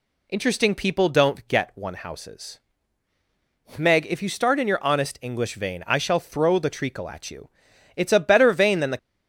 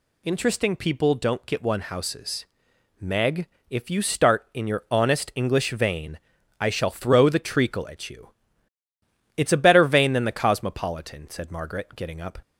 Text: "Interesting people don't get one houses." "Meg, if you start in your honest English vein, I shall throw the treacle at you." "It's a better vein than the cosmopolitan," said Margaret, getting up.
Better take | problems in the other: second | stops before "cosmopolitan said Margaret getting up"; at 8.9 s

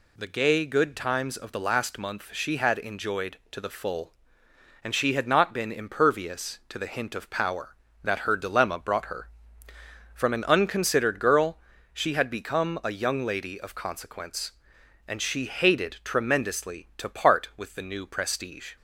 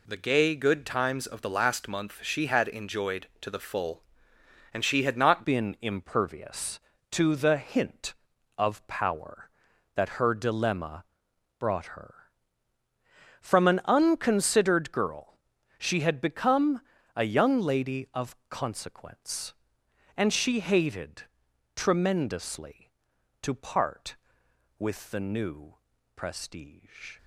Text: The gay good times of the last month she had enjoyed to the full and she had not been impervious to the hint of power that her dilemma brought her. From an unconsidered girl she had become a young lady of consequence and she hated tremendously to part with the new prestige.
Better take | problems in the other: first | changes voice at "been"; from 5.4 s on; 21.7 s long // pauses between "dilemma" and "brought"; noticeable; at 11.0 s; 0.52 s long // pauses between "girl" and "she"; noticeable; at 15.3 s; 0.46 s long; slight in the first // pauses between "become" and "a"; slight; at 16.8 s; 0.34 s long // pauses between "hated" and "tremendously"; noticeable; at 21.2 s; 0.52 s long // pauses between "new" and "prestige"; at 25.7 s; 0.42 s long

